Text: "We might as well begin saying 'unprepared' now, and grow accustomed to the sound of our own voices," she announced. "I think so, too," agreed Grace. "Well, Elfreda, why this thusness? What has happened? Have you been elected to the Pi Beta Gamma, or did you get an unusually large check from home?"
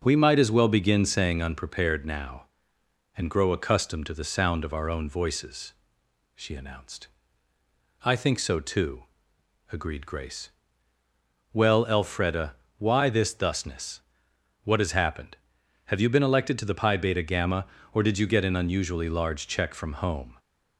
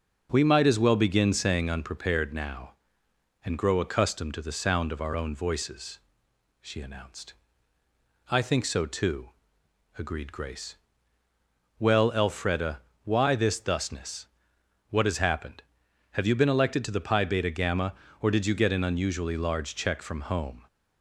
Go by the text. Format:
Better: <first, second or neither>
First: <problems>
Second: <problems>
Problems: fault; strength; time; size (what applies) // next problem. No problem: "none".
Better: neither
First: none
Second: none